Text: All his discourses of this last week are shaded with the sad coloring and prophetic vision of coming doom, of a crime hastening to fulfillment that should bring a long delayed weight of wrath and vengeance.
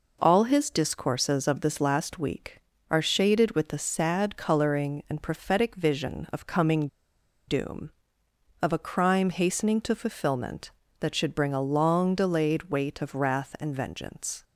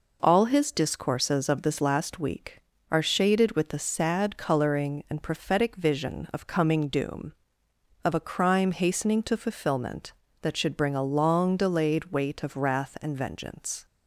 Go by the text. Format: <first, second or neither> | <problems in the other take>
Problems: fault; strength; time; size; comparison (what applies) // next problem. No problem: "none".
second | pauses between "coming" and "doom"; noticeable; at 6.8 s; 0.60 s long